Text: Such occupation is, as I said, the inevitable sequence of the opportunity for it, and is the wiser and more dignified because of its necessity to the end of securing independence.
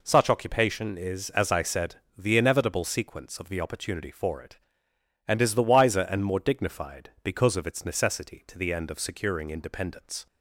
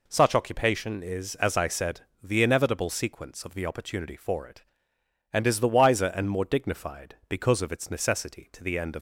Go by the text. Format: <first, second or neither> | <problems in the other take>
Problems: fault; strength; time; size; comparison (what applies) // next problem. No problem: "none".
first | stops before "securing independence"; at 8.9 s